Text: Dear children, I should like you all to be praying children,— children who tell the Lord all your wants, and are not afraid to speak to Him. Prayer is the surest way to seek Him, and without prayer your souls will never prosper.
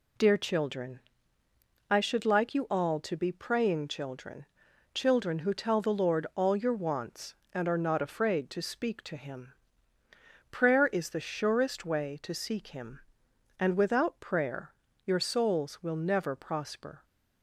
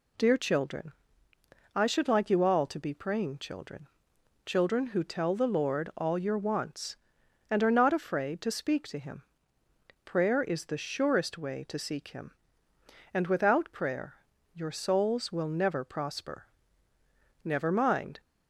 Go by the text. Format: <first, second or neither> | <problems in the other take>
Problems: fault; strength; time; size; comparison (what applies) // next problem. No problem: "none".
first | pauses between "prayer" and "your"; at 14.1 s; 0.40 s long; slight in the first // goes on to say "Never mind"; noticeable; from 17.4 s on; 0.76 s long